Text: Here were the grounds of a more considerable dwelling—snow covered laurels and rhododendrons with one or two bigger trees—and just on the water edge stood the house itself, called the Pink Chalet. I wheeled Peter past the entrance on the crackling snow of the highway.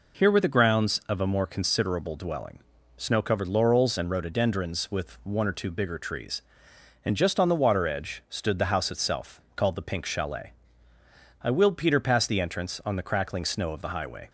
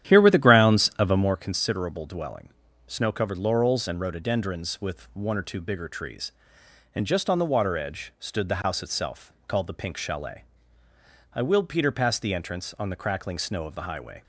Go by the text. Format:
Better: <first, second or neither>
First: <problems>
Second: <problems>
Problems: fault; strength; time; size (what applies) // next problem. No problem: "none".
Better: first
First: none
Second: starts louder than the rest; strong; until 1.5 s; 11 dB